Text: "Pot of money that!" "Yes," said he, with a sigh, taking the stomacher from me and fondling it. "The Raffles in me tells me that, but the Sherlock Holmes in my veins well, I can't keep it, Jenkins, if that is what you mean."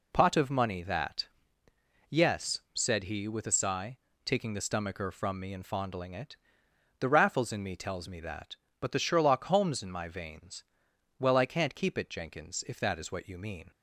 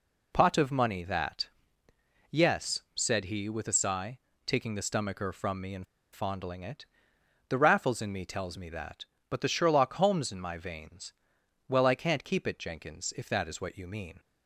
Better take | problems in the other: first | pauses between "and" and "fondling"; slight; at 5.8 s; 0.28 s long // pauses between "veins" and "well"; noticeable; at 11.1 s; 0.56 s long; noticeable in the first

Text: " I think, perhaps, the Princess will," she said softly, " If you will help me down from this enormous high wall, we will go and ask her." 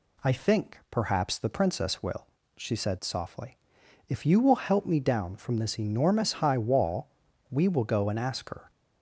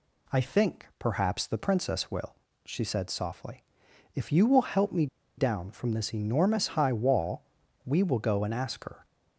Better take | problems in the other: first | pauses between "me" and "down"; slight; at 5.0 s; 0.31 s long

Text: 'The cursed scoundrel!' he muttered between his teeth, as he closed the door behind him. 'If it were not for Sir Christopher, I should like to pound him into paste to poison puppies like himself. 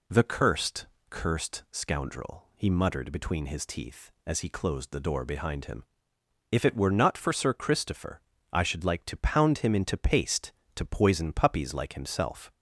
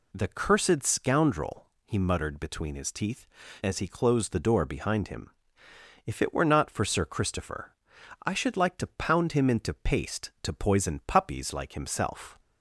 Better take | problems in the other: second | says "cursed" twice; at 1.0 s

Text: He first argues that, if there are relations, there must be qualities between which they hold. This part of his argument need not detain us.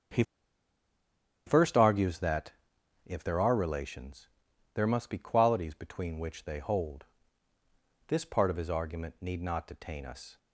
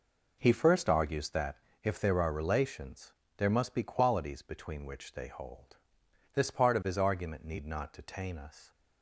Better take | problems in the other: second | starts louder than the rest; until 2.3 s; 7 dB // pauses between "He" and "first"; at 0.2 s; 1.2 s long

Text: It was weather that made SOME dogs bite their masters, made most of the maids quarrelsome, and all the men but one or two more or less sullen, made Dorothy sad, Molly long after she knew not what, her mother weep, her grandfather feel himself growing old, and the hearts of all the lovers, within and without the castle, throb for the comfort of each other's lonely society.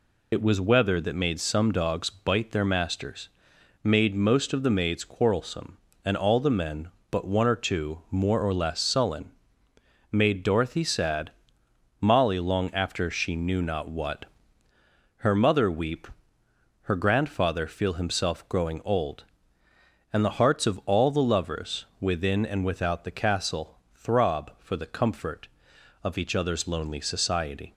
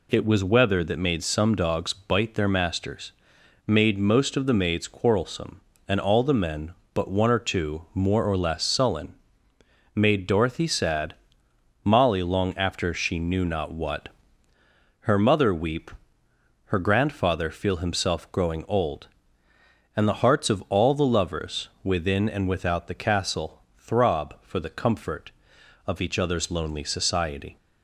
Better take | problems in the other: second | loses the start of "It"; at 0.3 s; 65 ms

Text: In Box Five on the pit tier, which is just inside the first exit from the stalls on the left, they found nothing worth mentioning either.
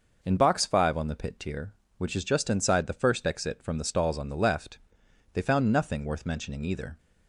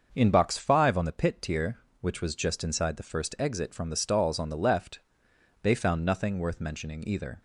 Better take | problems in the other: first | starts louder than the rest; until 1.1 s; 6.5 dB // says "was" for "is"; at 2.2 s

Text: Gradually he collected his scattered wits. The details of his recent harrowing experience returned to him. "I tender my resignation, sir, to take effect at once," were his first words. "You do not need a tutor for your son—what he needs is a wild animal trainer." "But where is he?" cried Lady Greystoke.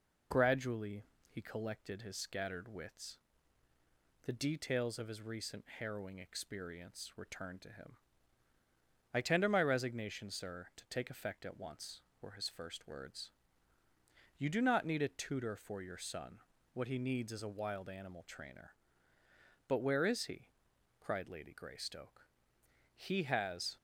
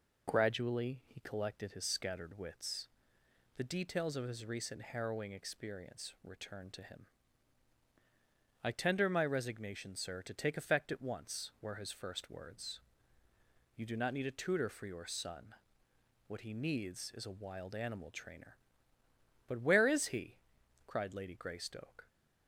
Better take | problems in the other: second | pauses between "Gradually" and "he"; slight; at 1.0 s; 0.24 s long // goes on to say "He has"; noticeable; from 22.9 s on; 0.80 s long

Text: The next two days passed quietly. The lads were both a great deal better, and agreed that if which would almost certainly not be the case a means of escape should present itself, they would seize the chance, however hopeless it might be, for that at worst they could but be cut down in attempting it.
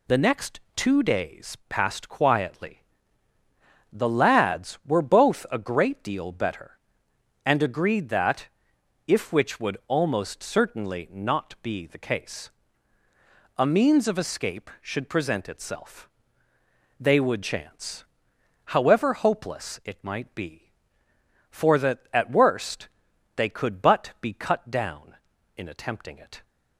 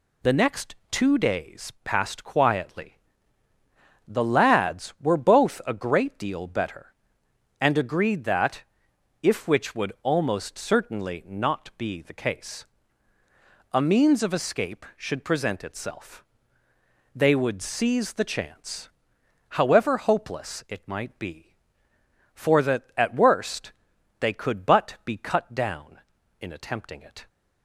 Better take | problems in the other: second | pauses between "next" and "two"; slight; at 0.6 s; 0.16 s long; slight in the second // pauses between "that" and "if"; noticeable; at 8.4 s; 0.62 s long; noticeable in the second // pauses between "case" and "a"; at 12.5 s; 1.0 s long; also in the second // skips "seize the"; at 17.4 s // pauses between "worst" and "they"; noticeable; at 22.8 s; 0.48 s long; noticeable in the second

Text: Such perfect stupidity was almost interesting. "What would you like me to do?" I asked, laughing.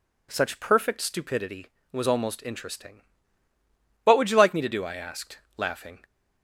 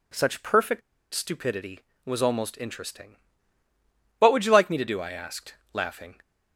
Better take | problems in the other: first | pauses between "perfect" and "stupidity"; slight; at 0.8 s; 0.33 s long

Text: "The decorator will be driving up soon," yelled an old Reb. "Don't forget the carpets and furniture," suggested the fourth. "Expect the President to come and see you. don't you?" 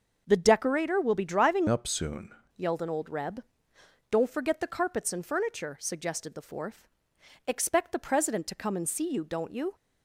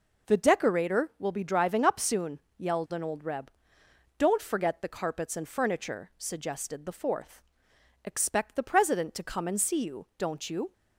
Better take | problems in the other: second | changes voice from "up" to "soon"; from 1.6 to 2.3 s; 0.7 s long

